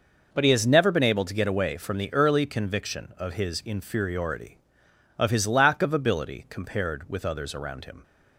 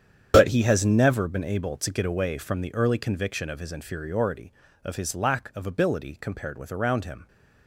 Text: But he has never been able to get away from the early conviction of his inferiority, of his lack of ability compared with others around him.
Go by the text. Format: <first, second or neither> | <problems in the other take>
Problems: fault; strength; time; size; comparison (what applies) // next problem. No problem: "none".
first | starts louder than the rest; strong; until 1.3 s; 8.5 dB // skips "others"; at 6.7 s